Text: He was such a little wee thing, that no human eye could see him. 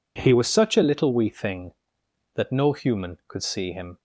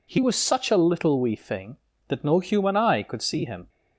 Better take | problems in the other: second | skips "eye"; at 3.2 s

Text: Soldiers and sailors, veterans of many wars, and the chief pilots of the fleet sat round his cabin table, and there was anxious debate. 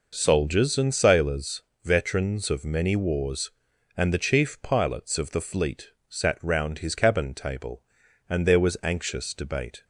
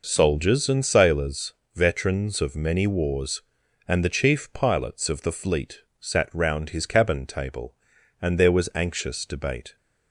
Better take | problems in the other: neither | pauses between "fleet" and "sat"; slight; the same in both

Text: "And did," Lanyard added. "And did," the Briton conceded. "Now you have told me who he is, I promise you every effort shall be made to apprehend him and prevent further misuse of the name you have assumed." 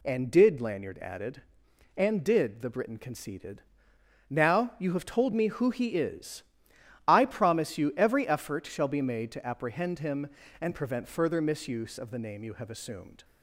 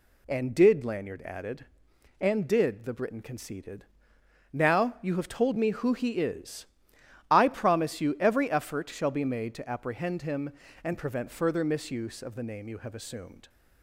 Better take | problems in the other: neither | none

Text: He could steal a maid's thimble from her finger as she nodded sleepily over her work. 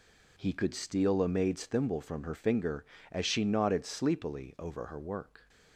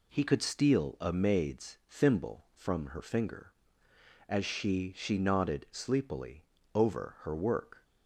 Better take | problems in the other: first | says "she" twice; at 4.9 s // pauses between "sleepily" and "over"; slight; at 6.4 s; 0.32 s long

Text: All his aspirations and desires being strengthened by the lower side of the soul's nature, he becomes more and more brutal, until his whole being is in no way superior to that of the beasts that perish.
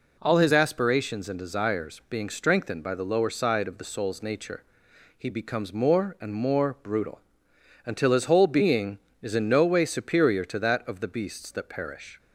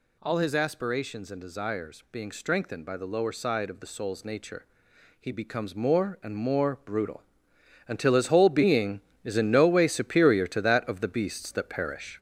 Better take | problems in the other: first | gets louder; noticeable; throughout; 5.5 dB

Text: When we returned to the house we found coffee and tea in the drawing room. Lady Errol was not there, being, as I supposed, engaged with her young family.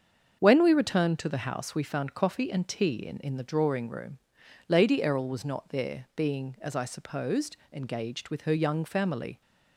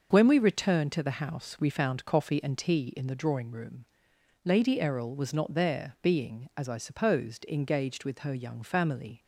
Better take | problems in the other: second | starts louder than the rest; until 1.4 s; 7 dB; noticeable in the second // says "in" twice; at 3.1 s

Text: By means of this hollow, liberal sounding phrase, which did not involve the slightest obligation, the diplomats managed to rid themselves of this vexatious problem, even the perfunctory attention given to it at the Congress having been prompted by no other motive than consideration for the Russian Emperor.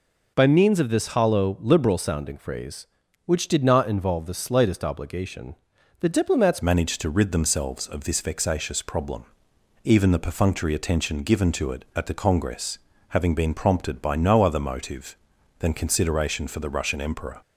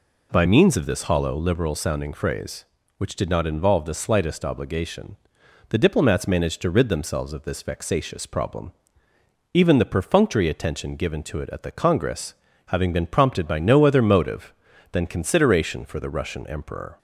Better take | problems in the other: second | changes voice at "managed"; from 6.6 s on; 10.8 s long // pauses between "Congress" and "having"; slight; at 12.7 s; 0.32 s long; slight in the second

